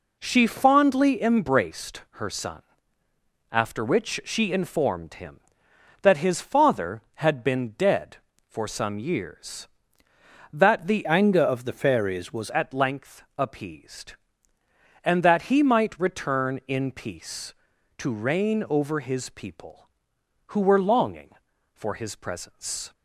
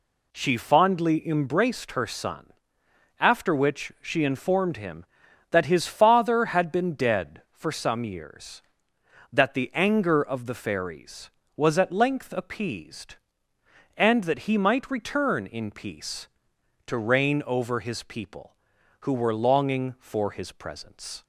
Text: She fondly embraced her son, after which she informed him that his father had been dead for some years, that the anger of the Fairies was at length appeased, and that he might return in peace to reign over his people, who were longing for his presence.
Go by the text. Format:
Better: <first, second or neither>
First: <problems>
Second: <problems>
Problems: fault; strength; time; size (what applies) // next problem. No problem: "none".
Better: second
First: changes voice from "anger" to "was"; from 11.0 to 12.5 s; 1.5 s long // pauses between "length" and "appeased"; slight; at 13.2 s; 0.16 s long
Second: none